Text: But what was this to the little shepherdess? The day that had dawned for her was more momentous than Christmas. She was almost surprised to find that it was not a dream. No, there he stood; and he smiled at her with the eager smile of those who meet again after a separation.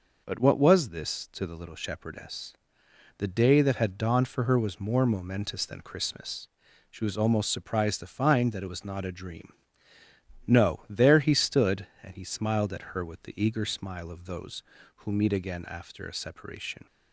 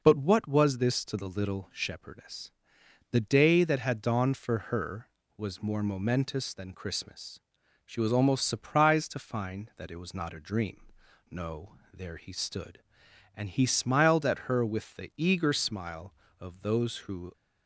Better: first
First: none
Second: stops before "meet again after a separation"; at 17.3 s

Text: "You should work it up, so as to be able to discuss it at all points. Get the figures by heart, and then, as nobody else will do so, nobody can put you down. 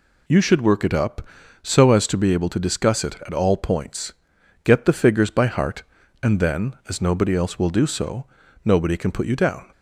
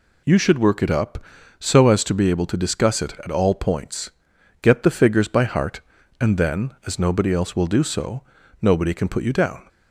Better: neither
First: none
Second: none

